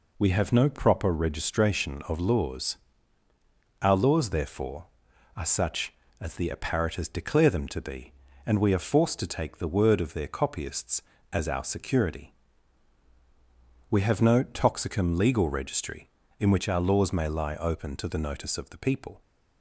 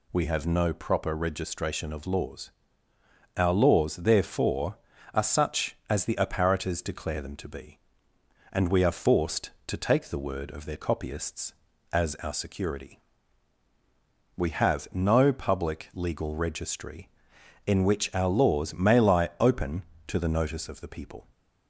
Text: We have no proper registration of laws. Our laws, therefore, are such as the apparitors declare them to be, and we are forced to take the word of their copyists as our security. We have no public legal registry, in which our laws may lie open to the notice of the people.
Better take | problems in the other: second | says "toxicum" for "public"; at 14.4 s

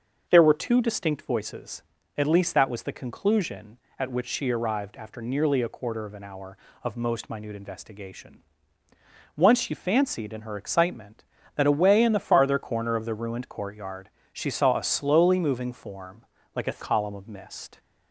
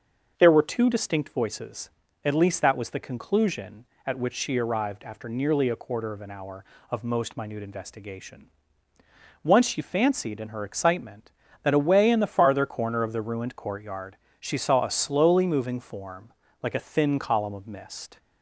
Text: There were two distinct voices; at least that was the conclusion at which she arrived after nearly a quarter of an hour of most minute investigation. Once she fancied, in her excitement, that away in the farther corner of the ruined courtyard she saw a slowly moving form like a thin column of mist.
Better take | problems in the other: second | starts louder than the rest; noticeable; until 1.3 s; 6 dB; also in the second // pauses between "courtyard" and "she"; slight; at 14.0 s; 0.24 s long; slight in the second // pauses between "form" and "like"; slight; at 16.2 s; 0.32 s long; slight in the second // skips "thin"; at 16.8 s

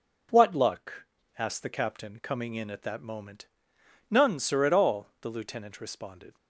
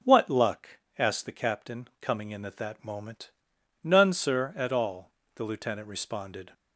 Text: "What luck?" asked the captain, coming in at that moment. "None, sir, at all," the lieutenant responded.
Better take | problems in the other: neither | none

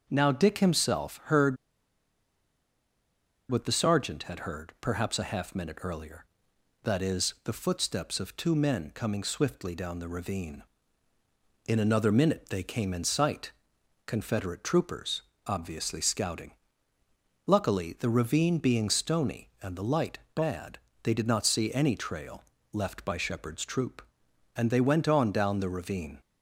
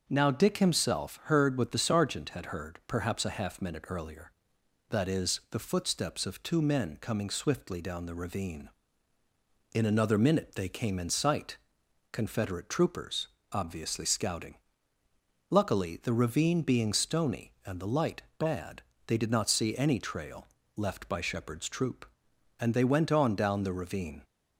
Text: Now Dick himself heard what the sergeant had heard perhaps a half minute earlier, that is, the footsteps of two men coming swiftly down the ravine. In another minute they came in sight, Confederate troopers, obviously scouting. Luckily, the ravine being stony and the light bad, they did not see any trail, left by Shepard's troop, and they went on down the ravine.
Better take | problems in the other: second | starts louder than the rest; until 1.1 s; 6.5 dB; also in the second // pauses between "heard" and "what"; strong; at 1.5 s; 1.9 s long // pauses between "light" and "bad"; slight; at 20.1 s; 0.16 s long; slight in the second

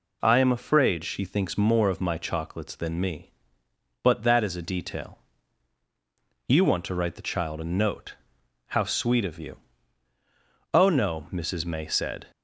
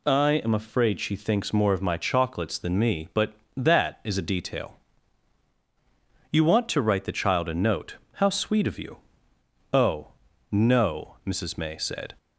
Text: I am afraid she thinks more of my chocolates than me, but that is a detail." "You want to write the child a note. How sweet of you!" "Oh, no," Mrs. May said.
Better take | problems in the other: neither | none

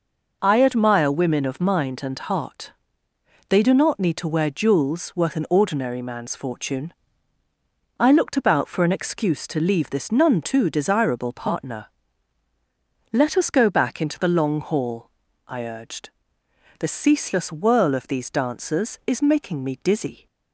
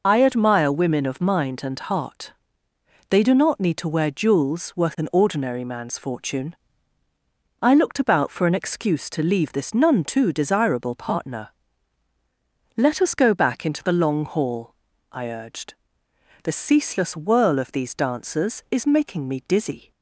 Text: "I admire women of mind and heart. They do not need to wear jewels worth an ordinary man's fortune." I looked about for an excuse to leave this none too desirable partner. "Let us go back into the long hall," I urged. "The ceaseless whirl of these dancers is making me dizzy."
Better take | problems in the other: first | loses the start of "I"; at 0.0 s; 25 ms

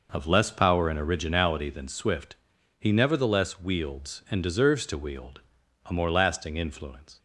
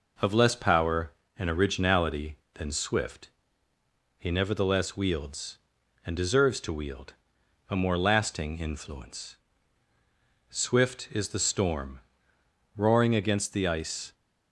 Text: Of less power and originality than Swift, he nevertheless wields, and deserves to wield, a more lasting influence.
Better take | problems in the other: first | goes on to say "Swift is the storm roaring against the ice"; strong; from 10.4 s on; 3.6 s long

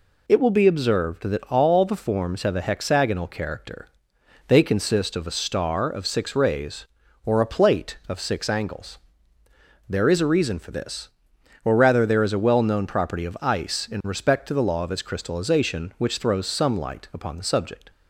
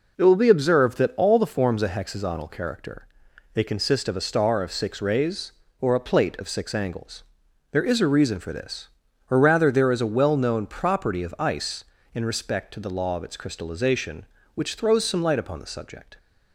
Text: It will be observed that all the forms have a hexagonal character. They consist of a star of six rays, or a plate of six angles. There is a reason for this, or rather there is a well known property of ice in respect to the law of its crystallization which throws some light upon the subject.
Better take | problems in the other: first | skips "have"; at 1.8 s

